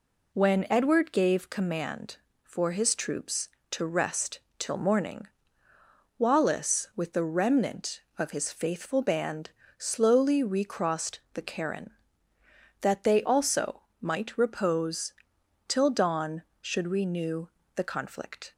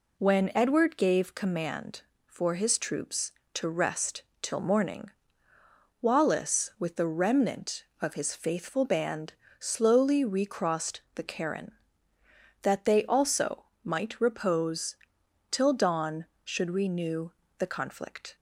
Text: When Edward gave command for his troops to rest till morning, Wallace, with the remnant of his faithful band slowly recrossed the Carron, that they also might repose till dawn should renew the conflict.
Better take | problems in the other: neither | pauses between "rest" and "till"; slight; the same in both // pauses between "band" and "slowly"; slight; the same in both // pauses between "also" and "might"; slight; the same in both // pauses between "repose" and "till"; noticeable; the same in both // pauses between "renew" and "the"; slight; the same in both

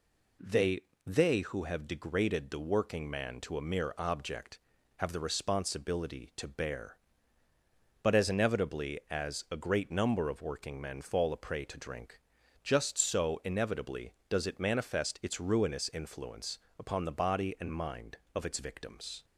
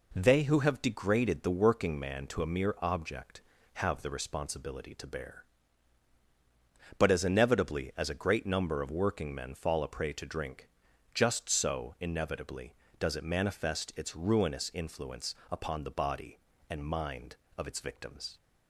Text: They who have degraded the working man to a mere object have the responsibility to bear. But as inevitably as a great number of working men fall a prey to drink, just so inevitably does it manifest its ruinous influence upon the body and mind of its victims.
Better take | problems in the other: second | says "They" twice; at 1.0 s // pauses between "influence" and "upon"; slight; at 16.5 s; 0.20 s long; slight in the second

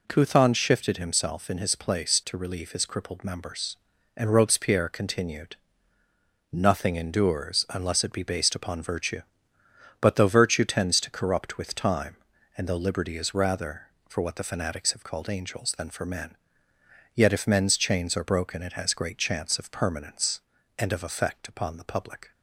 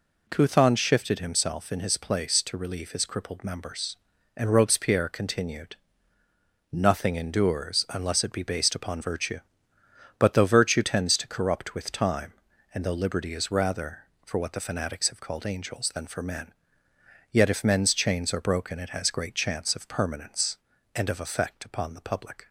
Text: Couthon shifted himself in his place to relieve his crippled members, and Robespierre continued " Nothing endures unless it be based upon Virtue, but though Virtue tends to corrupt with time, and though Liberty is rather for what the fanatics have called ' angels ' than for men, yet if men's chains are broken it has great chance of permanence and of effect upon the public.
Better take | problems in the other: neither | none

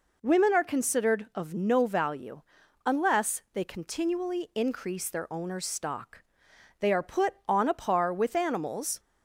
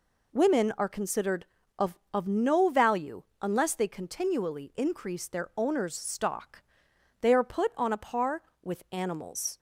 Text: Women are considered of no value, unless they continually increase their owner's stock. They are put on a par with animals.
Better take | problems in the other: first | says "of" twice; at 2.1 s

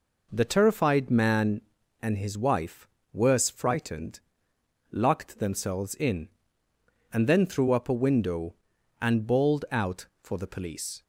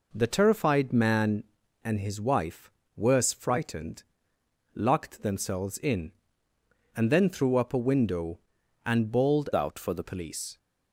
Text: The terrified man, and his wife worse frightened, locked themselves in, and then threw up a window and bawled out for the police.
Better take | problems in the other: first | pauses between "wife" and "worse"; slight; at 2.6 s; 0.28 s long; slight in the first // changes voice from "out" to "the"; from 9.5 to 10.0 s; 0.5 s long

